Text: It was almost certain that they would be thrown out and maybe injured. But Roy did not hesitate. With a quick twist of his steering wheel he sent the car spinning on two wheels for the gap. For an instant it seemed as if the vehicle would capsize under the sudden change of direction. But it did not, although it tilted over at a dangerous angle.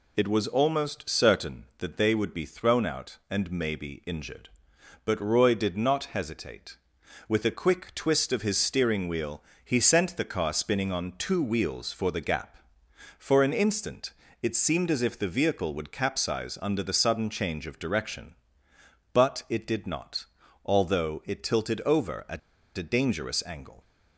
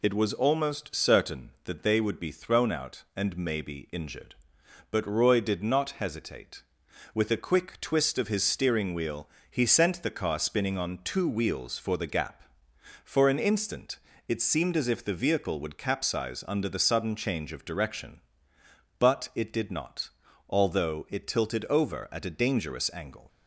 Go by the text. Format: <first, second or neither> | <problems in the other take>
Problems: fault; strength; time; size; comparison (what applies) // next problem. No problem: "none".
second | pauses between "wheel" and "he"; slight; at 9.4 s; 0.20 s long; slight in the second // pauses between "instant" and "it"; slight; at 14.1 s; 0.28 s long; slight in the second // pauses between "at" and "a"; at 22.3 s; 0.38 s long